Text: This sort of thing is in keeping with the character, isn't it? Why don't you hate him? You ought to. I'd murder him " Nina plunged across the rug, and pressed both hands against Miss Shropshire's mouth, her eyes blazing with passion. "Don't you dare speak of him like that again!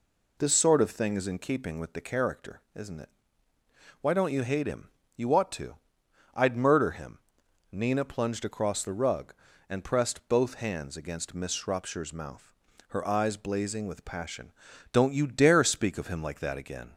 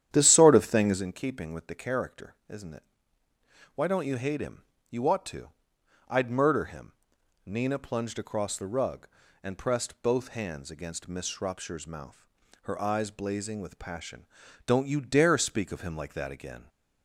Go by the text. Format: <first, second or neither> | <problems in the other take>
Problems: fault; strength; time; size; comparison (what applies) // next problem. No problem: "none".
first | starts louder than the rest; strong; until 1.0 s; 10 dB